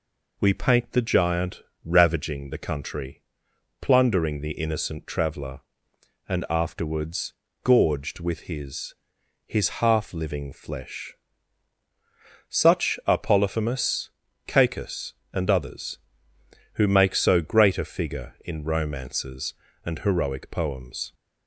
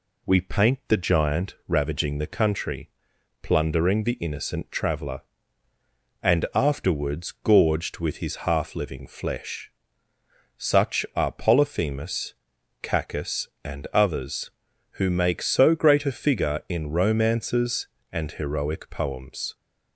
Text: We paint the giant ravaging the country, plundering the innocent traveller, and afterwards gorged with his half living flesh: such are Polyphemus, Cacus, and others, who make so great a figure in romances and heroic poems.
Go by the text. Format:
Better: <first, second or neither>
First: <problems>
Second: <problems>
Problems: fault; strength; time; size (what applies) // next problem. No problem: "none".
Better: second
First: pauses between "giant" and "ravaging"; slight; at 1.6 s; 0.24 s long // pauses between "afterwards" and "gorged"; slight; at 7.3 s; 0.32 s long // says "his" twice; at 9.4 s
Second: none